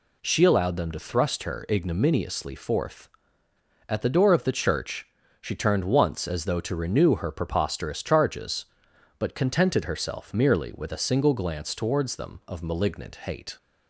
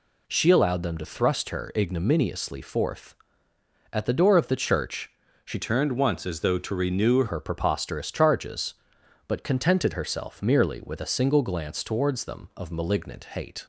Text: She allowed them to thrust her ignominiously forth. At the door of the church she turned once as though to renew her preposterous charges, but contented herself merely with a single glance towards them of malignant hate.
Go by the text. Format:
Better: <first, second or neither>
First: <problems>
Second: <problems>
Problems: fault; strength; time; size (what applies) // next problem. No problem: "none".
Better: first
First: pauses between "church" and "she"; slight; at 5.0 s; 0.34 s long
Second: pauses between "church" and "she"; slight; at 5.1 s; 0.34 s long // changes voice from "turned" to "renew"; from 5.6 to 7.2 s; 1.6 s long